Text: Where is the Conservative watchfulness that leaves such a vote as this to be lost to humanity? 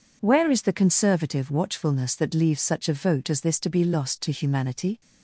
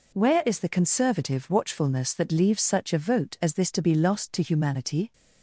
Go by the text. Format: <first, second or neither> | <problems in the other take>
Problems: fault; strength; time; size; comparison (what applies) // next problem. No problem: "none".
neither | none